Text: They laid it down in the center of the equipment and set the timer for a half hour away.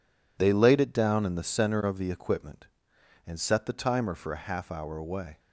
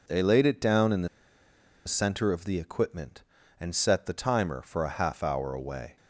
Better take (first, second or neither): first